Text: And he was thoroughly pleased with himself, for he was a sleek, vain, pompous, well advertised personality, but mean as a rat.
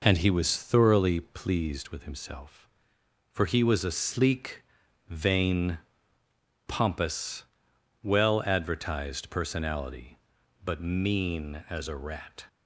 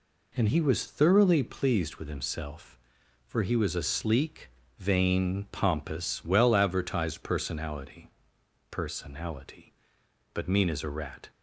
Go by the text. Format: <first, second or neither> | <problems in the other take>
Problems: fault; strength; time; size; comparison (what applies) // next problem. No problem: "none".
first | says "personality" twice; at 8.7 s